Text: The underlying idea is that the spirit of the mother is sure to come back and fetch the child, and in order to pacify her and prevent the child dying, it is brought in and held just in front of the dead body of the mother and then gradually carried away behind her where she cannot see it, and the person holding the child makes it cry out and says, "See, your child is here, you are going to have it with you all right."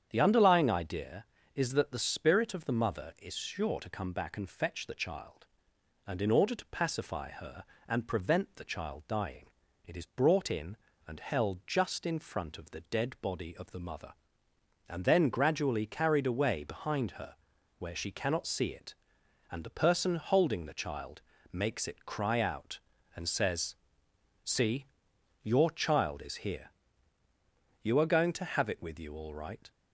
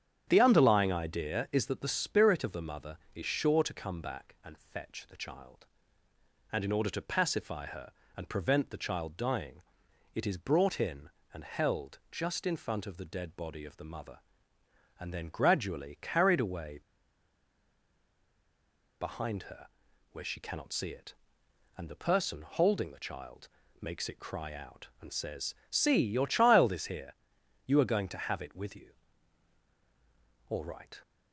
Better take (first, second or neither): first